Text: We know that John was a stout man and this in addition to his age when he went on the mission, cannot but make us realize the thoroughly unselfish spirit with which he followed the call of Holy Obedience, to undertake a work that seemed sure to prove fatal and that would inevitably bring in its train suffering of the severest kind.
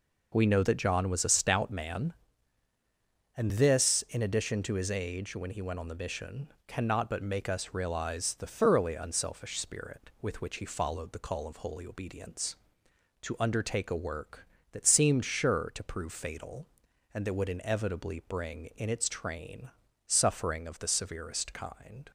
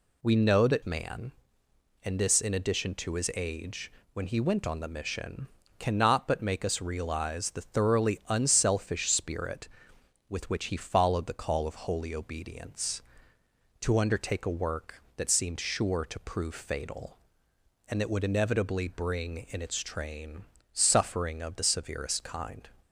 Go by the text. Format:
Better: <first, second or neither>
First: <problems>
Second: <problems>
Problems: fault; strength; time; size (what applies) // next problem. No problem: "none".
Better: first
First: pauses between "train" and "suffering"; slight; at 19.7 s; 0.36 s long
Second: skips "John was a stout"; at 0.8 s // pauses between "age" and "when"; slight; at 3.9 s; 0.22 s long // pauses between "train" and "suffering"; slight; at 20.4 s; 0.30 s long